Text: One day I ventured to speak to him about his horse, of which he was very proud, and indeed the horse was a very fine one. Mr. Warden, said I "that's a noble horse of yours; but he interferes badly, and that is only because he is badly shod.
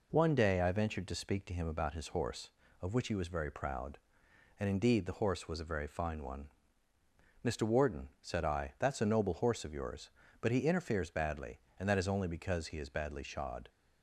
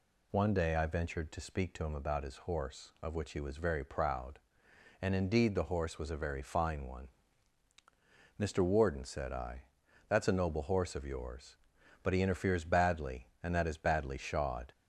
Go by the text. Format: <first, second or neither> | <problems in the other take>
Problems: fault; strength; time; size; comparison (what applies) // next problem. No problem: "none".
first | pauses between "I" and "that's"; at 9.6 s; 0.44 s long // skips "is only because he"; at 13.6 s